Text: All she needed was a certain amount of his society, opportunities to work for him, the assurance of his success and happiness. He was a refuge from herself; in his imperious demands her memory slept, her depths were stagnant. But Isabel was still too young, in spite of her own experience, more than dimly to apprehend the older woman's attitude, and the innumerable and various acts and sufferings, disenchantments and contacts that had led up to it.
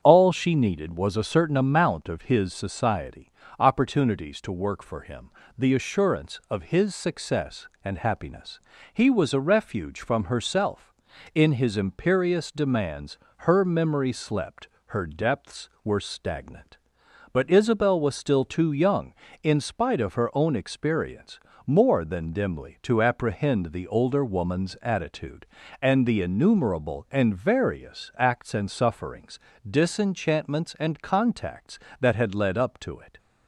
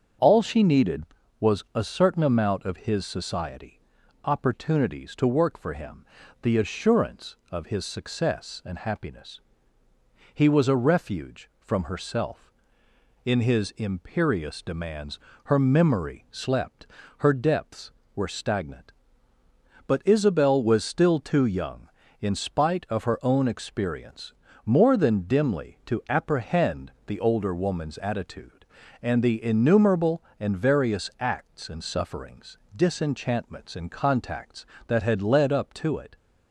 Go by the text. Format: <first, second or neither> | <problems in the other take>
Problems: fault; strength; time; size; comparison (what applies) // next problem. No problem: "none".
neither | starts louder than the rest; the same in both // pauses between "demands" and "her"; slight; the same in both